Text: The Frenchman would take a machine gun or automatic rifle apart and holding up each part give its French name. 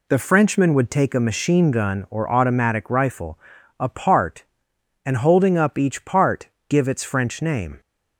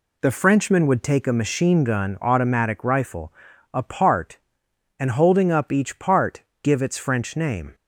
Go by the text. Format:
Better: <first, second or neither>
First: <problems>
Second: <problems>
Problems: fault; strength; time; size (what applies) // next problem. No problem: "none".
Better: first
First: pauses between "rifle" and "apart"; at 3.3 s; 0.40 s long // pauses between "part" and "give"; slight; at 6.4 s; 0.20 s long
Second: skips "or"; at 2.2 s // pauses between "rifle" and "apart"; at 3.3 s; 0.40 s long // pauses between "part" and "give"; slight; at 6.4 s; 0.20 s long